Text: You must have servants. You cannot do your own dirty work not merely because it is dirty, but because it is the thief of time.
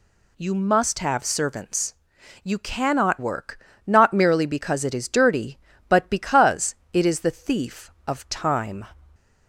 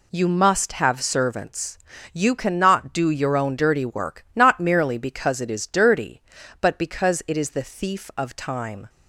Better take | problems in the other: second | skips "do your own dirty"; at 3.1 s // pauses between "work" and "not"; slight; at 3.5 s; 0.28 s long // pauses between "because" and "it"; slight; at 6.7 s; 0.16 s long

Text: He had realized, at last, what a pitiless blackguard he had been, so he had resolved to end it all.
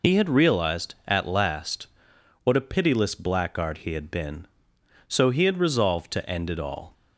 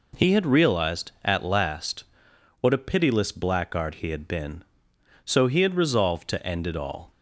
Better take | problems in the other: second | loses the start of "He"; at 0.0 s; 80 ms

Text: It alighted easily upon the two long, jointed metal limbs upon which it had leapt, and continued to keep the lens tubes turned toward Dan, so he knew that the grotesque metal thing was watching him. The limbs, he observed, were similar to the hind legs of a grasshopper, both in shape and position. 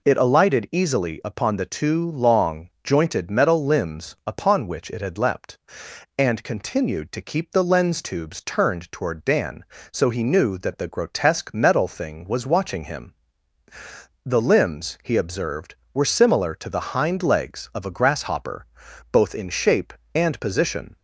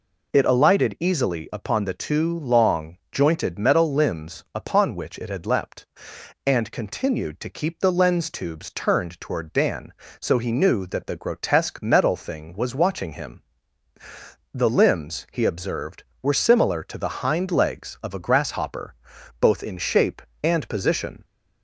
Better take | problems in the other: neither | none

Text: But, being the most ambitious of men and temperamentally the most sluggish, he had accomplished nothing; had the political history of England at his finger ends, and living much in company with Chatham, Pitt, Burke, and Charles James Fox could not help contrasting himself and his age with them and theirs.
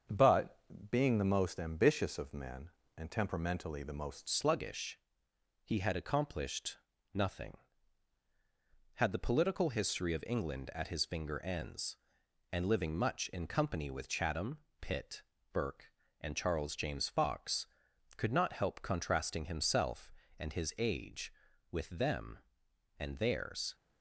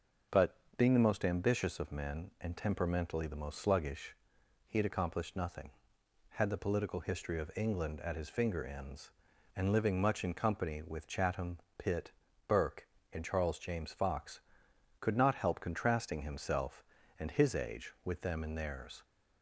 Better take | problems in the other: second | starts louder than the rest; strong; until 1.4 s; 7 dB // changes voice at "sluggish"; from 4.2 s on; 19.5 s long // pauses between "accomplished" and "nothing"; slight; at 6.7 s; 0.36 s long

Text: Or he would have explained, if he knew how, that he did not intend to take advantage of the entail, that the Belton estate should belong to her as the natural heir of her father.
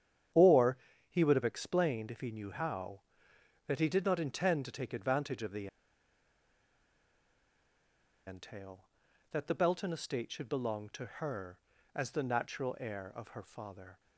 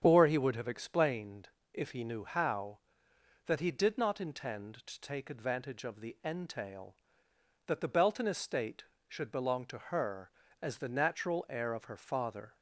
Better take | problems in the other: second | starts louder than the rest; strong; until 1.6 s; 9 dB; strong in the second // pauses between "Or" and "he"; slight; at 0.7 s; 0.32 s long // pauses between "the" and "entail"; strong; at 5.6 s; 2.6 s long

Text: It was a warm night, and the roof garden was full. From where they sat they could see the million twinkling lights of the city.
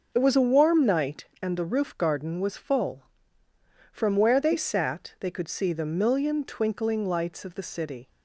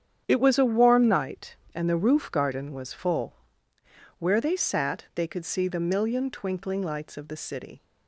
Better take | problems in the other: first | starts louder than the rest; strong; until 1.2 s; 8.5 dB // skips "From"; at 3.7 s

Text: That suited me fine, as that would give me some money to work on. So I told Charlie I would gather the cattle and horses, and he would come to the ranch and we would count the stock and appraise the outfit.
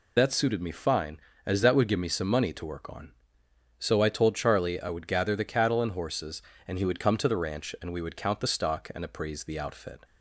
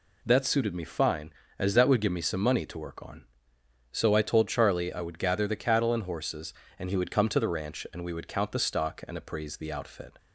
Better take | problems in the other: second | loses the start of "That"; at 0.1 s; 50 ms

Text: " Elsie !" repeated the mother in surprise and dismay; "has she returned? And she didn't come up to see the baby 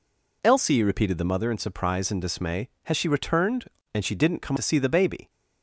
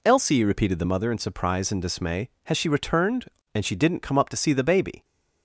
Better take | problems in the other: second | skips "up"; at 4.5 s

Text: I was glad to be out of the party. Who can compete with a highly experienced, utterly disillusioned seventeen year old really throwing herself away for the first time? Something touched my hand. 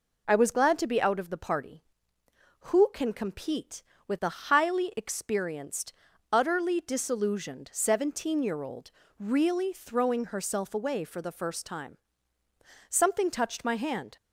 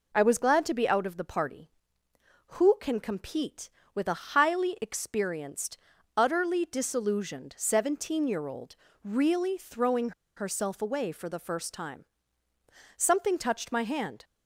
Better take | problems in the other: first | pauses between "old" and "really"; slight; at 8.7 s; 0.28 s long; slight in the first // pauses between "throwing" and "herself"; slight; at 10.1 s; 0.25 s long

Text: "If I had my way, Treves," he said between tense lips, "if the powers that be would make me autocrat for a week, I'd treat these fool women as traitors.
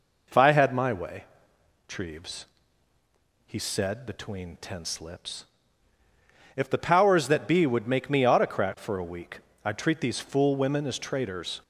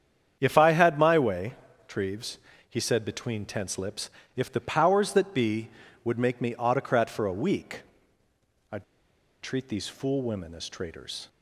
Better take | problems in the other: first | starts louder than the rest; strong; until 1.4 s; 8.5 dB // pauses between "I'd" and "treat"; noticeable; at 8.8 s; 0.58 s long

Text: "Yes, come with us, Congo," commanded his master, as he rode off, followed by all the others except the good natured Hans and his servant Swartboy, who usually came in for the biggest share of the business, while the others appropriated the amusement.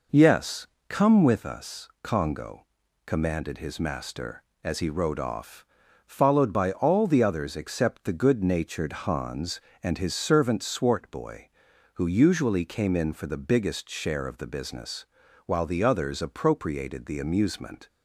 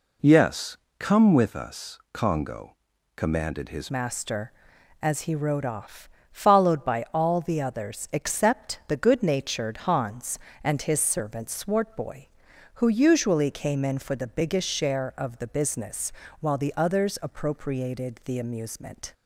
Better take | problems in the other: first | changes voice at "master"; from 3.9 s on; 15.2 s long

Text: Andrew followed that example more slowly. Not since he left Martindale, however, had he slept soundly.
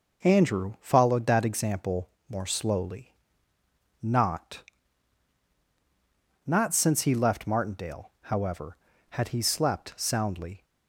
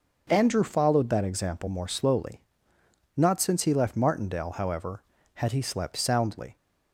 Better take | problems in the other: second | pauses between "example" and "more"; slight; at 2.1 s; 0.18 s long // says "Not" twice; at 6.4 s

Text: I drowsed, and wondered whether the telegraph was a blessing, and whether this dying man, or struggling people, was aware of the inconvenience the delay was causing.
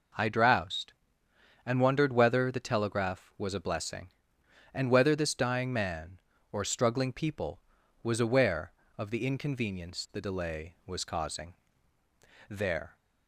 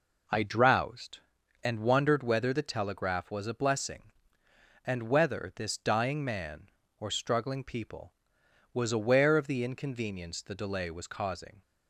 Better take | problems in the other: second | goes on to say "There"; slight; from 12.4 s on; 0.48 s long

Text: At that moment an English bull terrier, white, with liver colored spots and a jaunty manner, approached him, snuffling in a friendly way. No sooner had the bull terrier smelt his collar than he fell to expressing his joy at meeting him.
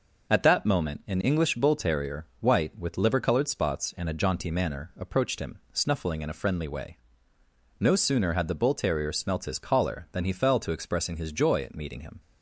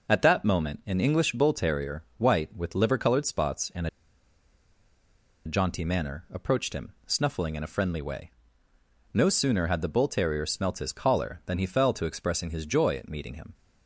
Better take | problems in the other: first | pauses between "and" and "a"; strong; at 3.8 s; 1.5 s long

